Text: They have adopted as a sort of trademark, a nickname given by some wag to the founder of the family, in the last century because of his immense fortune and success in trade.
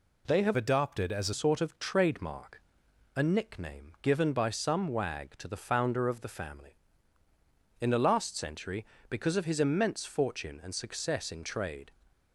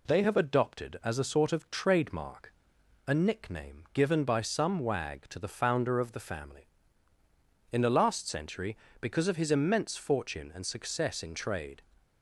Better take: second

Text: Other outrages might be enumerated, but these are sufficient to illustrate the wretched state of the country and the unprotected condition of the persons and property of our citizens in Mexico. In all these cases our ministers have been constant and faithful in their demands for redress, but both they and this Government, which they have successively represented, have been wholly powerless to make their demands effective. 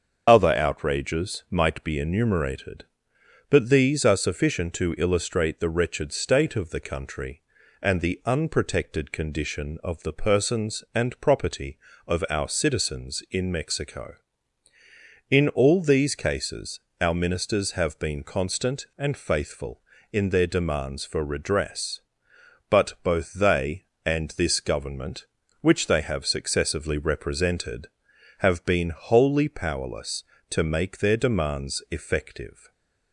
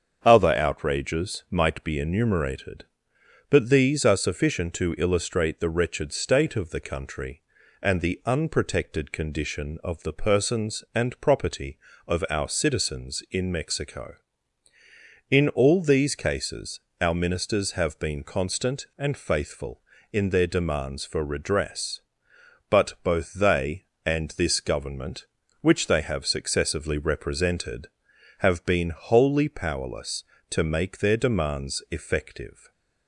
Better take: second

